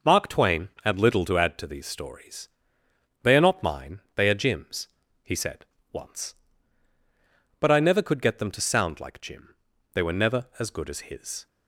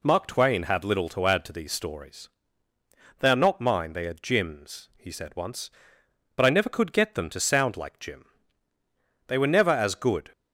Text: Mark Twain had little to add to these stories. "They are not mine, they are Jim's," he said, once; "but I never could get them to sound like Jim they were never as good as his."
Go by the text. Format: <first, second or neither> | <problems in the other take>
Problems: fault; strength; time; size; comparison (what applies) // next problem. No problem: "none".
first | pauses between "Jim" and "they"; at 8.2 s; 1.0 s long; also in the first // stops before "as his"; at 10.3 s